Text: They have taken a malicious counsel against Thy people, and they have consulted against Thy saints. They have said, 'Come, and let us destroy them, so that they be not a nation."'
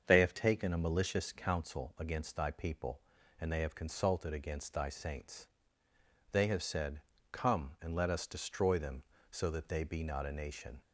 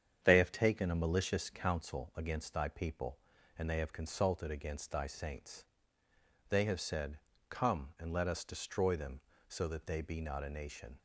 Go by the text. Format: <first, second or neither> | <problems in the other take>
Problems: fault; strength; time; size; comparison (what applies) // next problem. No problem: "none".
first | gets quieter; noticeable; throughout; 4.5 dB // starts louder than the rest; strong; until 1.2 s; 8 dB; also in the first